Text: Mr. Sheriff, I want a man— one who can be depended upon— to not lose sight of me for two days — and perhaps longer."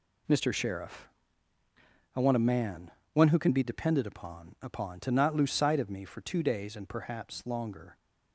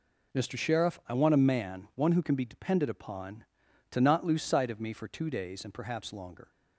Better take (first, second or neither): second